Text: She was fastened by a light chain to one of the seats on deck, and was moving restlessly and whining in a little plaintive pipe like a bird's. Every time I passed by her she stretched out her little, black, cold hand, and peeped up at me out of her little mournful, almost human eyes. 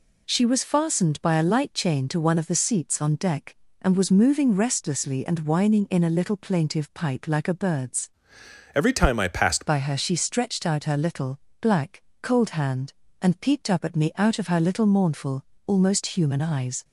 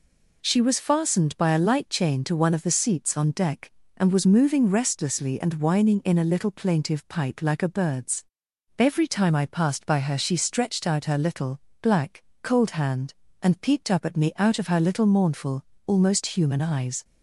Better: second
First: changes voice from "Every" to "passed"; from 8.7 to 9.6 s; 0.9 s long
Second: none

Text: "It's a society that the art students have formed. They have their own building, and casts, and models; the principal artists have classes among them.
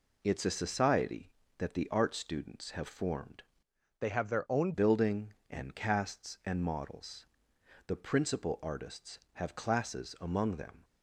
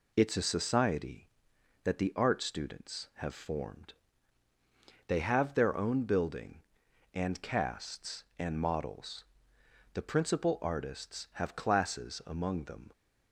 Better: second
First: changes voice from "They" to "own"; from 3.9 to 4.7 s; 0.8 s long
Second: none

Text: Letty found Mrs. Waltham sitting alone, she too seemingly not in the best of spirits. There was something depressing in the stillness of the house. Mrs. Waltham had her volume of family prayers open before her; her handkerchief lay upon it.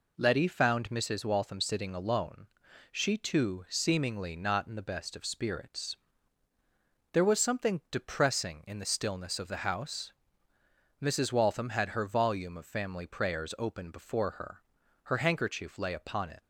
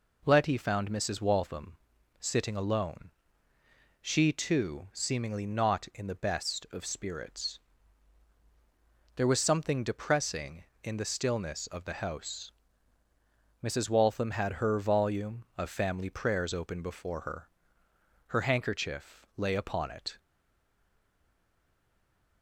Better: first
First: none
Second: pauses between "Waltham" and "sitting"; at 1.7 s; 0.44 s long // stays silent after the last word; from 20.1 s on; 2.3 s long

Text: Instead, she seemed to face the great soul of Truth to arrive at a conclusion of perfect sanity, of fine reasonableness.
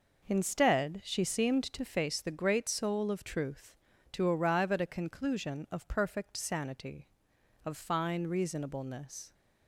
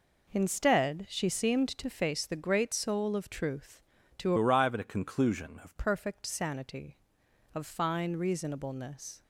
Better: first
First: none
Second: changes voice from "arrive" to "of"; from 4.3 to 5.7 s; 1.4 s long

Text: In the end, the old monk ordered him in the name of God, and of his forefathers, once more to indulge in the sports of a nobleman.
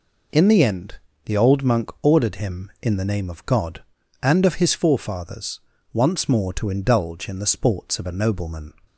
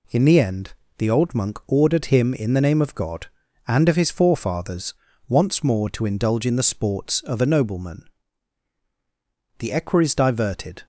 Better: first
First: none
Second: goes on to say "The equerries diverted"; noticeable; from 9.5 s on; 1.2 s long

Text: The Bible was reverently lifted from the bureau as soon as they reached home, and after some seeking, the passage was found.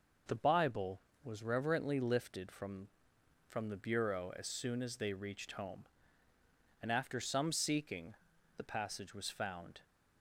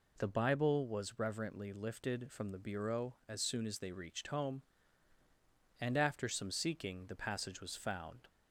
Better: second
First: says "from" twice; at 3.4 s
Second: none

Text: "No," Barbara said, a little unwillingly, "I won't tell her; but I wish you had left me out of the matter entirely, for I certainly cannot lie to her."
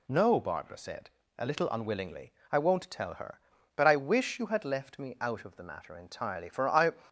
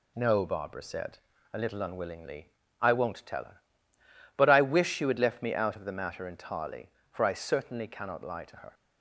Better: second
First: stops before "certainly cannot lie to her"; at 7.0 s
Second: none

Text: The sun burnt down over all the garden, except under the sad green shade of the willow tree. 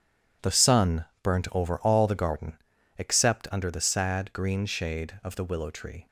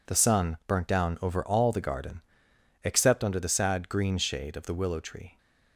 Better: second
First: starts louder than the rest; strong; until 1.6 s; 9.5 dB // pauses between "sun" and "burnt"; slight; at 1.0 s; 0.18 s long // skips "down"; at 1.5 s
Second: none

